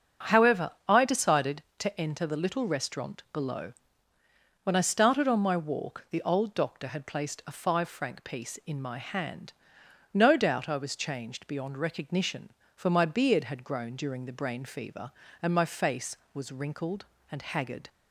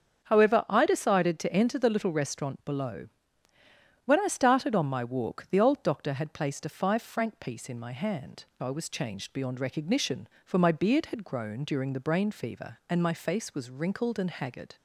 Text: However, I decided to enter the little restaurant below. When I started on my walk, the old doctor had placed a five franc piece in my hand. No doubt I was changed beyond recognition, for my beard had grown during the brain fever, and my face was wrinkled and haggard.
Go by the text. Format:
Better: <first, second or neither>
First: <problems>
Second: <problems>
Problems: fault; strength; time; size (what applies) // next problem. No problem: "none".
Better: first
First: starts louder than the rest; until 1.4 s; 7 dB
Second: starts louder than the rest; until 1.2 s; 7 dB // skips "No doubt"; at 8.5 s